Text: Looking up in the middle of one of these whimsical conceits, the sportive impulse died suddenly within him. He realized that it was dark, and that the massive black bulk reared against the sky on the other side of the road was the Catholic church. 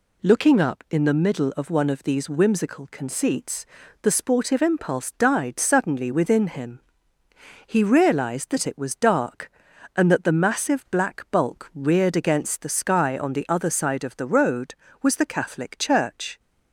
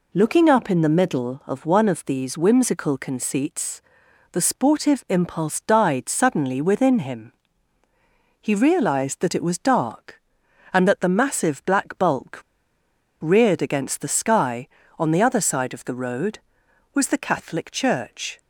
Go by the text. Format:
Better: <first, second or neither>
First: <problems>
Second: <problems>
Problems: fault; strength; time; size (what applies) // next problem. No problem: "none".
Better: first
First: none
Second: pauses between "bulk" and "reared"; noticeable; at 12.3 s; 0.81 s long